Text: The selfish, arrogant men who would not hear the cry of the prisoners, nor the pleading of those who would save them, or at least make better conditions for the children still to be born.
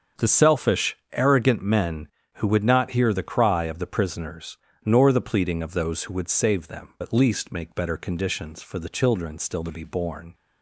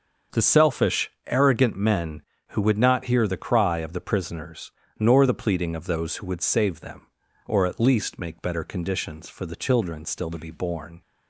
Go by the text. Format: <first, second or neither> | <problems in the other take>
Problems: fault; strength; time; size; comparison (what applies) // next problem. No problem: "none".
second | starts louder than the rest; until 1.3 s; 7 dB; also in the second // skips "or"; at 6.9 s